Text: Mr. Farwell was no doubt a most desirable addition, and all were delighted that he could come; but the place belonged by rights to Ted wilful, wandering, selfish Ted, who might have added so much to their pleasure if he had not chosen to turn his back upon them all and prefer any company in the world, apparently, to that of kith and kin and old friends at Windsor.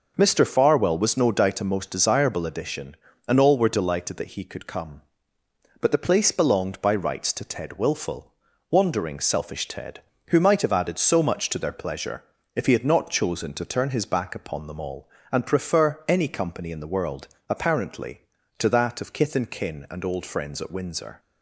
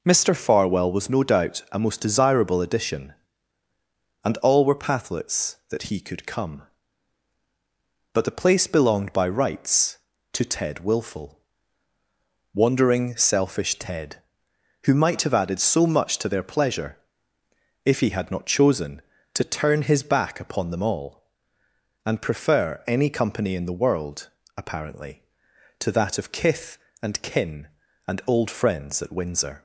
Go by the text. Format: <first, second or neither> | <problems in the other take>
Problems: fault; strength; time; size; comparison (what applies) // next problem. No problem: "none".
first | says "pathlets" for "delighted"; at 4.8 s // pauses between "pleasure" and "if"; noticeable; at 16.9 s; 0.88 s long; slight in the first